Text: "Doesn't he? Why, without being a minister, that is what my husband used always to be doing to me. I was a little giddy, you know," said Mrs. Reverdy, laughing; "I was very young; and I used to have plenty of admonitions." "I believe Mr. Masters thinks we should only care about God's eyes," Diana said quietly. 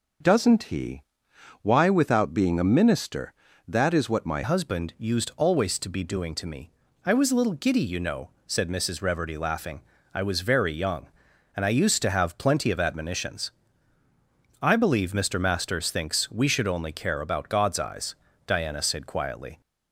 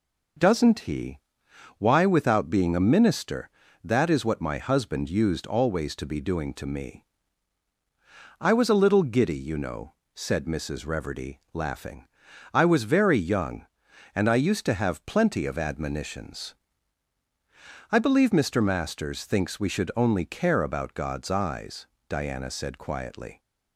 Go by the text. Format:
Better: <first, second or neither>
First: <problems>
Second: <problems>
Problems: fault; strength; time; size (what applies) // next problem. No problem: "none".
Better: second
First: changes voice at "husband"; from 4.4 s on; 15.2 s long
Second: none